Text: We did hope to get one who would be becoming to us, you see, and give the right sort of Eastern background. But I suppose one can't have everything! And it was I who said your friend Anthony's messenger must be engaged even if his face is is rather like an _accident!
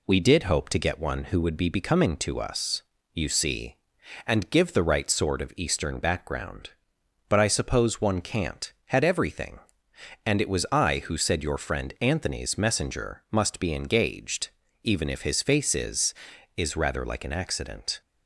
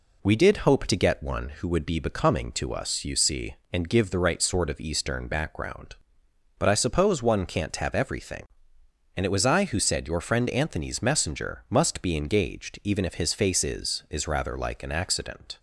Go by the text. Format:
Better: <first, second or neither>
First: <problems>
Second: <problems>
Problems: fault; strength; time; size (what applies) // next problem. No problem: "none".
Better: second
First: says "had" for "have"; at 8.8 s // pauses between "engaged" and "even"; slight; at 14.4 s; 0.34 s long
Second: none